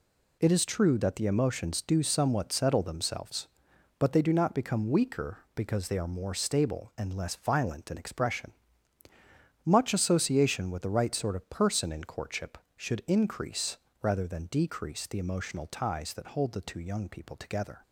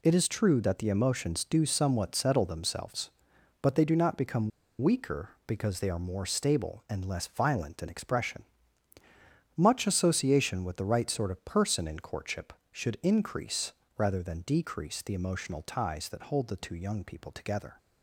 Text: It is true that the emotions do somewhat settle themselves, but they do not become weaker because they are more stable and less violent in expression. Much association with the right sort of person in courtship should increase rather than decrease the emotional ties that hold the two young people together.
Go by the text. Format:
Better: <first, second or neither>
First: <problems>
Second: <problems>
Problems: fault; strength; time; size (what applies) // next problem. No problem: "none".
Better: first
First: pauses between "increase" and "rather"; slight; at 13.7 s; 0.26 s long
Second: pauses between "become" and "weaker"; slight; at 4.5 s; 0.31 s long // pauses between "increase" and "rather"; slight; at 13.7 s; 0.26 s long